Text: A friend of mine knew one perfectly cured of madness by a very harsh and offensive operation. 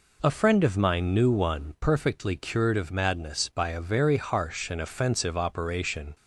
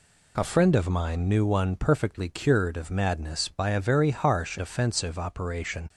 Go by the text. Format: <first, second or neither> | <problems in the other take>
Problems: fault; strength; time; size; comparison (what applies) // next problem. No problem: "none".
first | skips "and"; at 4.5 s